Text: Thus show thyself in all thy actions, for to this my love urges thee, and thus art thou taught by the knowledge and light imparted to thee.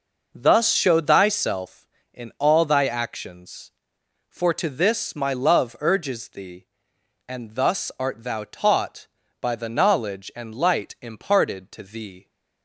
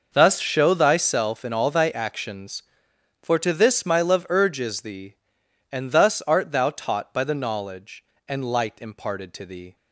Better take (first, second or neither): neither